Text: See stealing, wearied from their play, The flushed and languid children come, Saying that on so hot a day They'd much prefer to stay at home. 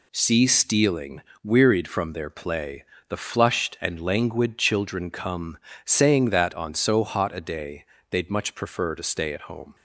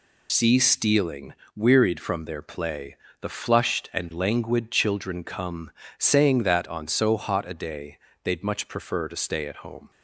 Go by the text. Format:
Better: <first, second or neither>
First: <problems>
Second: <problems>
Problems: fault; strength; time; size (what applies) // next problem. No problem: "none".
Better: first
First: pauses between "day" and "They'd"; slight; at 7.8 s; 0.24 s long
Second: loses the start of "See"; at 0.2 s; 70 ms // pauses between "day" and "They'd"; slight; at 7.9 s; 0.24 s long